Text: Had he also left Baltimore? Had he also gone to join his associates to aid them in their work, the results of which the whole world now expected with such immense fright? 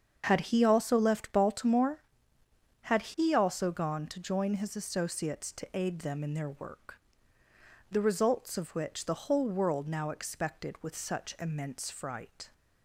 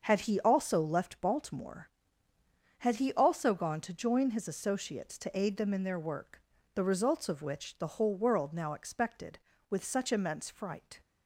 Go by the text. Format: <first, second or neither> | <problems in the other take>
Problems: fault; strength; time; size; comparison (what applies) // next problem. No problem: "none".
neither | starts louder than the rest; the same in both